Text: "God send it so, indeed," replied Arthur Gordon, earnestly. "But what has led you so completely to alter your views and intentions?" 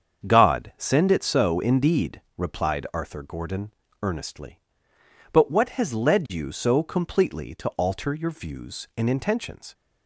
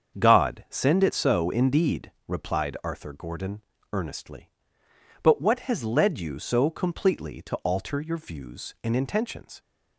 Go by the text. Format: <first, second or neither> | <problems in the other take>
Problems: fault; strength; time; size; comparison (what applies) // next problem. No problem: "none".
neither | starts louder than the rest; strong; the same in both